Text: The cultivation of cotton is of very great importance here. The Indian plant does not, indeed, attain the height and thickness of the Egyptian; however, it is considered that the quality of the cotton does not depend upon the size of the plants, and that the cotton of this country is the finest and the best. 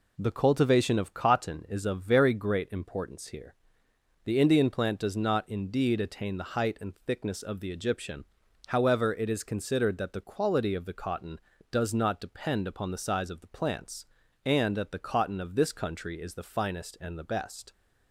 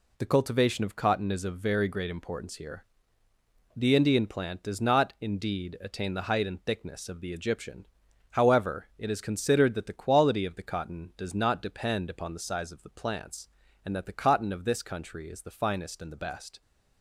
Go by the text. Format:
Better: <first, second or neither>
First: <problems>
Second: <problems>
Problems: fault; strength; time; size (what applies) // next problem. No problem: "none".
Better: neither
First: none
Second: none